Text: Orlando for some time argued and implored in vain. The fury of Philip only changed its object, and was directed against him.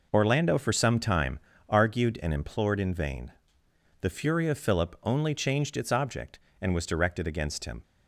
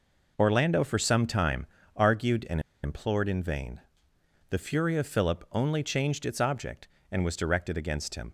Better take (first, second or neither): first